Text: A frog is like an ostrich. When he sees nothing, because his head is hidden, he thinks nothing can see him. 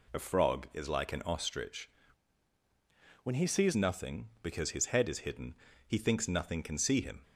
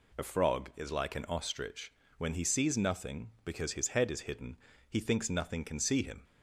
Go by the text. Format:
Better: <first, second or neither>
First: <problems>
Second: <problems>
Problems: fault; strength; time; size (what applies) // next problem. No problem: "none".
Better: second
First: changes voice from "When" to "sees"; from 3.2 to 3.7 s; 0.5 s long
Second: none